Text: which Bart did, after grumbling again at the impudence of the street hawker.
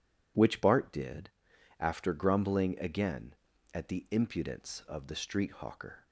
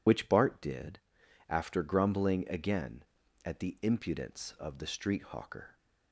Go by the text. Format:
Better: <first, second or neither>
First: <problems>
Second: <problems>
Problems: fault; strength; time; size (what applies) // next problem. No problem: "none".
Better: first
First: none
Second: loses the start of "which"; at 0.0 s; 55 ms